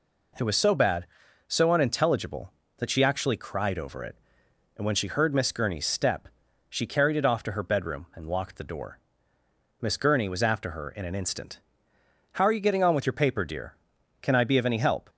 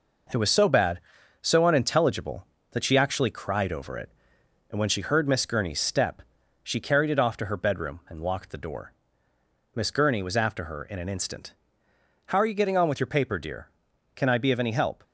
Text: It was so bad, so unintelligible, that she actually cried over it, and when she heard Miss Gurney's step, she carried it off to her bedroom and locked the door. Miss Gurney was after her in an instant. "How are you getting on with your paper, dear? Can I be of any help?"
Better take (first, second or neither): first